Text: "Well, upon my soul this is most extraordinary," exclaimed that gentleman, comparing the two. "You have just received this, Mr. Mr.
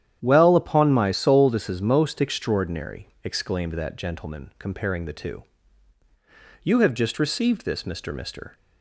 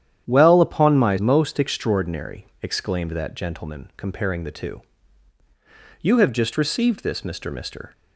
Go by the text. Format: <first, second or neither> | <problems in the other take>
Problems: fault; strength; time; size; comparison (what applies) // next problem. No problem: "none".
first | starts louder than the rest; strong; until 1.3 s; 10 dB; strong in the first // skips "soul this is"; at 1.1 s